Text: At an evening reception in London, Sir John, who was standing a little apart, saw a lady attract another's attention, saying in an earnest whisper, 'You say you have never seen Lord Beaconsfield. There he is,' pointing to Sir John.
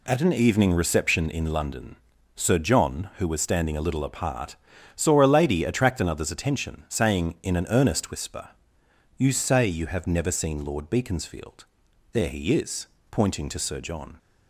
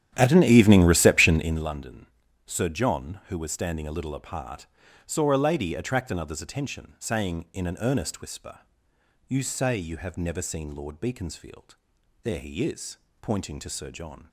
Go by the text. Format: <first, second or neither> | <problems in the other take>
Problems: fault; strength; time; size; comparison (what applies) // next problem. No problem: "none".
first | starts louder than the rest; strong; until 1.7 s; 10 dB